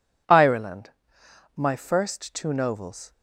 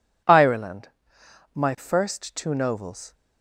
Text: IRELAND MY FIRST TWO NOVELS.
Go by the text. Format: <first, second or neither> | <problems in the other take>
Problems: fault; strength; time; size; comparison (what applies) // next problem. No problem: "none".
neither | pauses between "IRELAND" and "MY"; noticeable; the same in both